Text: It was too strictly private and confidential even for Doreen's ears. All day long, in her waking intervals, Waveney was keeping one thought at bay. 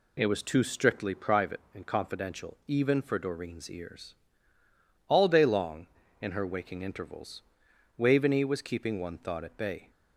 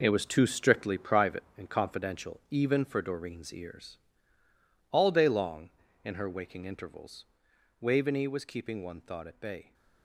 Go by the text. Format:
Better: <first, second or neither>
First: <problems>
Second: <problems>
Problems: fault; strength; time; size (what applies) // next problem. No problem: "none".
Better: first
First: none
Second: gets quieter; strong; throughout; 10 dB